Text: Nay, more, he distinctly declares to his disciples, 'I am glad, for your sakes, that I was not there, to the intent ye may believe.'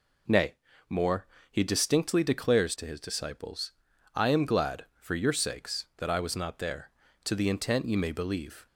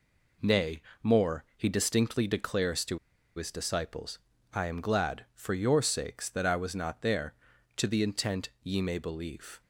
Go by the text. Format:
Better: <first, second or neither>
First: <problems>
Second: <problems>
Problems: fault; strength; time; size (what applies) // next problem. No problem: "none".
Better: first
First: none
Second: pauses between "to" and "his"; at 2.9 s; 0.37 s long